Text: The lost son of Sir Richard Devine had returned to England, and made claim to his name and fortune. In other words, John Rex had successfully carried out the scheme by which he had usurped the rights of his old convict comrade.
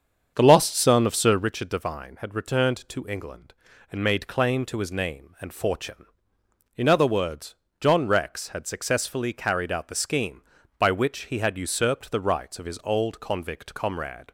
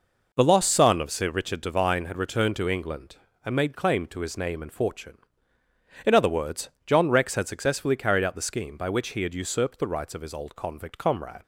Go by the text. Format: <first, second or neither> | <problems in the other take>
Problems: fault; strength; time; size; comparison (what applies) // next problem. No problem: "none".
second | starts louder than the rest; strong; until 1.5 s; 7 dB